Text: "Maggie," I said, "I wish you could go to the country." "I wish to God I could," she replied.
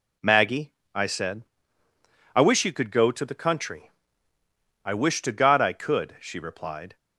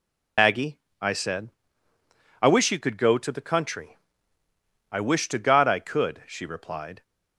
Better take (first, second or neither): first